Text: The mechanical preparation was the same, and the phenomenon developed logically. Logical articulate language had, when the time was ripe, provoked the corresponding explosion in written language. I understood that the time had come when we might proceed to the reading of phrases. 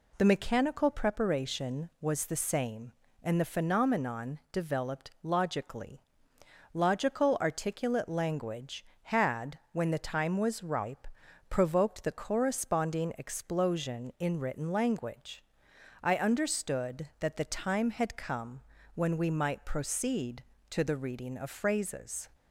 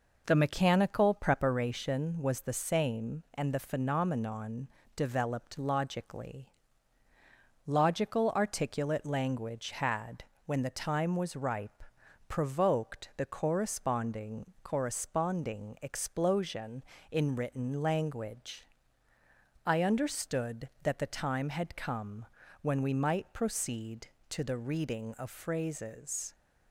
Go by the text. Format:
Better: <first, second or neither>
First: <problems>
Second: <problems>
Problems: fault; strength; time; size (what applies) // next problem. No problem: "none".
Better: first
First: pauses between "come" and "when"; slight; at 18.6 s; 0.34 s long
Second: pauses between "phenomenon" and "developed"; slight; at 4.6 s; 0.28 s long // says "corresponding" twice; at 14.6 s // pauses between "come" and "when"; at 22.2 s; 0.38 s long